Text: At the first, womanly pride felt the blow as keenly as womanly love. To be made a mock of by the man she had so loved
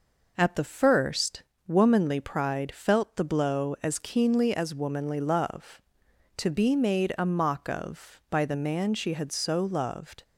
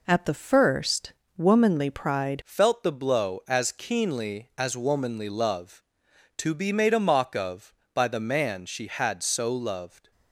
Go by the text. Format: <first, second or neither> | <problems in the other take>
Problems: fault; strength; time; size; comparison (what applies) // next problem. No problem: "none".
first | changes voice at "felt"; from 2.4 s on; 7.7 s long